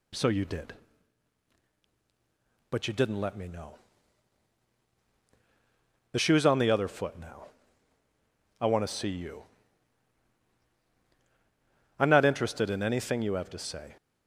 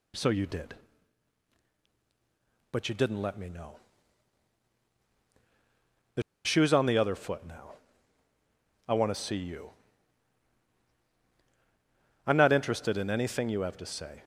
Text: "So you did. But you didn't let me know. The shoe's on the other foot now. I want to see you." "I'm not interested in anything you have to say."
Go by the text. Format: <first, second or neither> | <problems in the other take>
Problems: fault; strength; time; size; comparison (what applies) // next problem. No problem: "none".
first | pauses between "The" and "shoe's"; slight; at 6.2 s; 0.23 s long